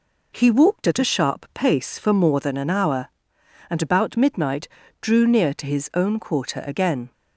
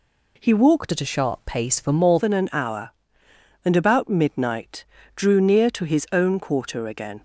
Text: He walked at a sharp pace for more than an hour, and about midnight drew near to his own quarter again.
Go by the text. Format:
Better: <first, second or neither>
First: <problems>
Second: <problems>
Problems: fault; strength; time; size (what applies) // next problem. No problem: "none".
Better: first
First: pauses between "midnight" and "drew"; slight; at 4.6 s; 0.32 s long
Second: changes voice from "at" to "more"; from 0.9 to 2.1 s; 1.2 s long // pauses between "midnight" and "drew"; slight; at 4.8 s; 0.30 s long